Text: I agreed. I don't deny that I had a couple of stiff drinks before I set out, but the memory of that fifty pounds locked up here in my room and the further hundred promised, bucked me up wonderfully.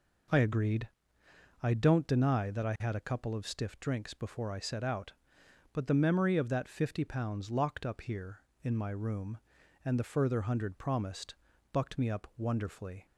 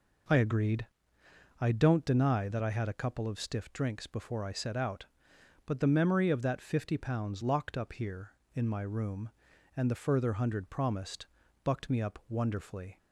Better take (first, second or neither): neither